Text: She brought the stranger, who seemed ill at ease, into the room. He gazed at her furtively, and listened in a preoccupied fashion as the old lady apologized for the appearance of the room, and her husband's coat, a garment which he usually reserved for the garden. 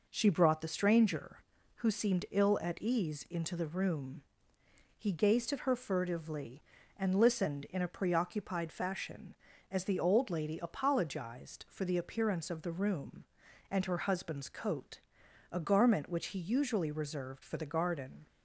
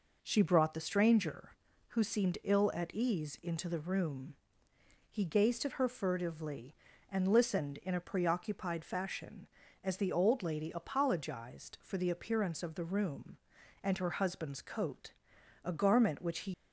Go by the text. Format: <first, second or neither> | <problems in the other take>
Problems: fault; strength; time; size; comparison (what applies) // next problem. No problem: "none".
first | stops before "usually reserved for the garden"; at 16.5 s